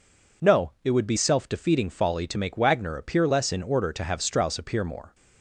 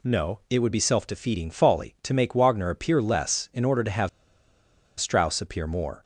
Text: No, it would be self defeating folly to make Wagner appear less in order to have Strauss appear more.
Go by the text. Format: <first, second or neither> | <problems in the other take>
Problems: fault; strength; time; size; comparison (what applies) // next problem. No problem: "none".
first | pauses between "have" and "Strauss"; noticeable; at 4.0 s; 0.89 s long